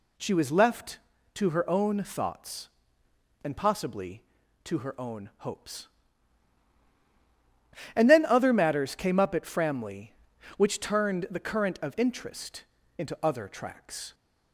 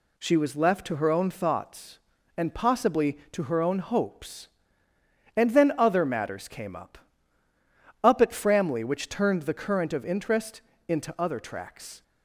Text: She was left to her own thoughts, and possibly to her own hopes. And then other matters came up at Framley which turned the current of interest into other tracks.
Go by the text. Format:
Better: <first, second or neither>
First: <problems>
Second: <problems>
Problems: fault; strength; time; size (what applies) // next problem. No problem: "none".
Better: first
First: pauses between "interest" and "into"; slight; at 12.6 s; 0.32 s long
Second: says "up" twice; at 8.0 s // pauses between "interest" and "into"; slight; at 10.6 s; 0.26 s long